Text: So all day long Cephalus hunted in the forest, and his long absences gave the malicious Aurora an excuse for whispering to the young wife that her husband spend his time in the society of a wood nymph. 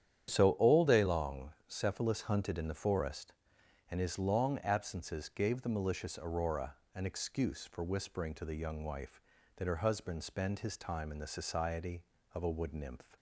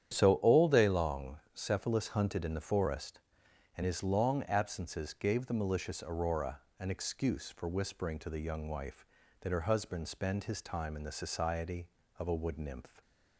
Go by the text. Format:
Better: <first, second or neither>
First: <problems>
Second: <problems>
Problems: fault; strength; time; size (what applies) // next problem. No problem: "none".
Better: neither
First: starts louder than the rest; strong; until 1.3 s; 9.5 dB // pauses between "long" and "Cephalus"; slight; at 1.5 s; 0.16 s long // pauses between "Aurora" and "an"; slight; at 6.7 s; 0.22 s long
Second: starts louder than the rest; strong; until 1.2 s; 9.5 dB // pauses between "long" and "Cephalus"; slight; at 1.3 s; 0.16 s long // pauses between "Aurora" and "an"; slight; at 6.5 s; 0.22 s long